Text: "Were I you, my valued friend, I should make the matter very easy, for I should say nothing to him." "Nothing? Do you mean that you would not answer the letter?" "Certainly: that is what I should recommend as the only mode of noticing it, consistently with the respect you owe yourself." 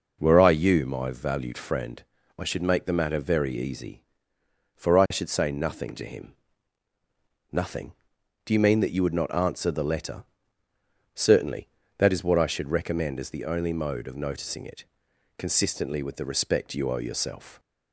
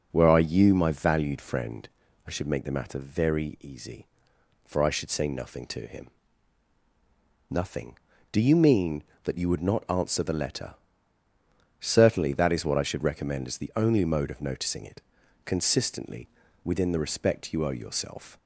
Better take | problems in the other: first | says "within" for "with"; at 16.6 s

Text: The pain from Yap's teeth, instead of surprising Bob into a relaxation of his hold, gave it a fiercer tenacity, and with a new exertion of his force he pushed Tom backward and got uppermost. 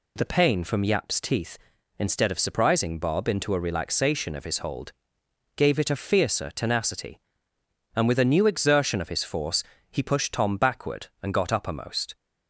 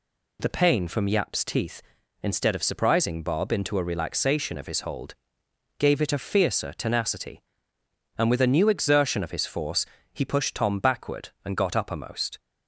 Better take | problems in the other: neither | pauses between "force" and "he"; slight; the same in both

